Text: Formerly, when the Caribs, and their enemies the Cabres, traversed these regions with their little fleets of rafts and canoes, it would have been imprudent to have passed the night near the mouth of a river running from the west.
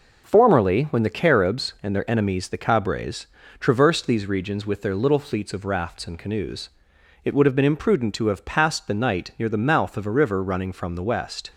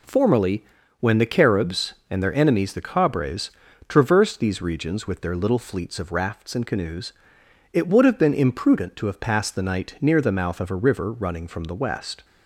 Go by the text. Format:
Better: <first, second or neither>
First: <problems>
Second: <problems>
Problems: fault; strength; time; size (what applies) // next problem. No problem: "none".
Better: neither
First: none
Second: none